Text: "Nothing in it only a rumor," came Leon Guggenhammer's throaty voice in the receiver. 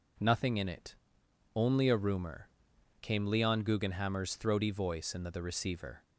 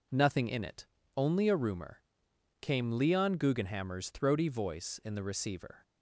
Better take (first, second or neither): second